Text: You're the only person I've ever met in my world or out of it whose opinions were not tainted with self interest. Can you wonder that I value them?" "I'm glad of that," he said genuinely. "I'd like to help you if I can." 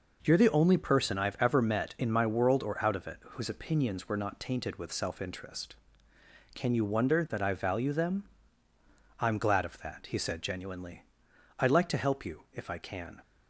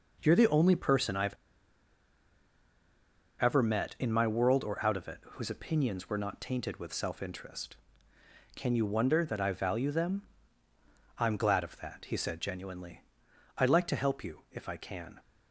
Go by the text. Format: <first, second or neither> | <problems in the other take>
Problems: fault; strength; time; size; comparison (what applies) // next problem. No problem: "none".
first | pauses between "I've" and "ever"; strong; at 1.3 s; 2.0 s long